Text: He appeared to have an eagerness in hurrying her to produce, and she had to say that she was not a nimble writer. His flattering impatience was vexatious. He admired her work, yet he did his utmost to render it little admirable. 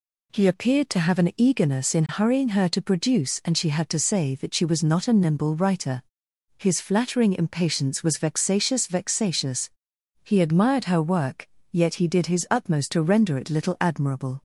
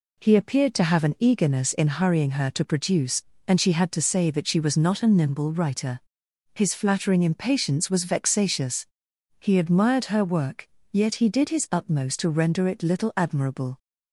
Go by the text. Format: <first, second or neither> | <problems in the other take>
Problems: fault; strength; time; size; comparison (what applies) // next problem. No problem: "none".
second | says "vexatious" twice; at 8.8 s